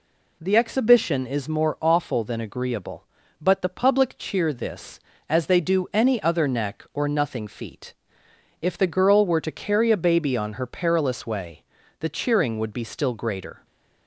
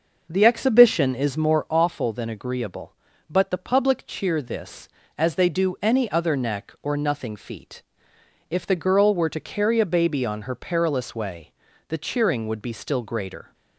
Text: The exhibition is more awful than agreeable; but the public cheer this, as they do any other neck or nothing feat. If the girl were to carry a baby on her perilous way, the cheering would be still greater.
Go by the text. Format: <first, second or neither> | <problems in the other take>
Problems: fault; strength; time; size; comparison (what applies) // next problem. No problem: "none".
first | starts louder than the rest; noticeable; until 1.8 s; 6 dB